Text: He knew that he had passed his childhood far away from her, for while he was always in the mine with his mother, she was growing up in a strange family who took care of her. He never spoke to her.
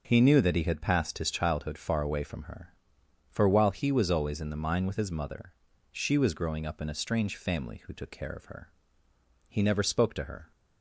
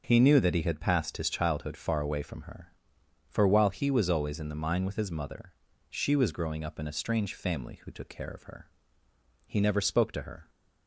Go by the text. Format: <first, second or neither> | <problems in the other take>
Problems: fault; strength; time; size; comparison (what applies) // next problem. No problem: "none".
neither | none